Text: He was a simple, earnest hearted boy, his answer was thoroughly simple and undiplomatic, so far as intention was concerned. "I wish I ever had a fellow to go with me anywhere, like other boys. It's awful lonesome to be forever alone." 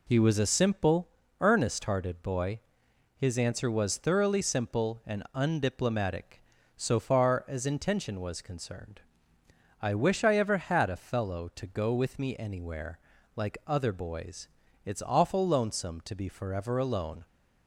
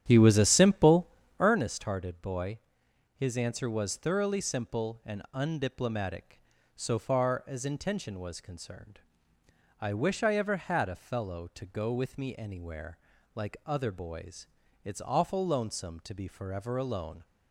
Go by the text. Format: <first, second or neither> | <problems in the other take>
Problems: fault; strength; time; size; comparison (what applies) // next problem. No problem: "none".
first | starts louder than the rest; strong; until 1.6 s; 10 dB